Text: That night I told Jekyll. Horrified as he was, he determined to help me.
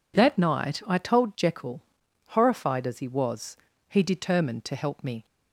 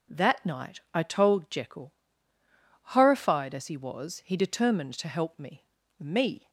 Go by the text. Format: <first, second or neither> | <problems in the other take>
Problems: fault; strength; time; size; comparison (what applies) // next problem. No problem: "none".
first | says "me" twice; at 5.9 s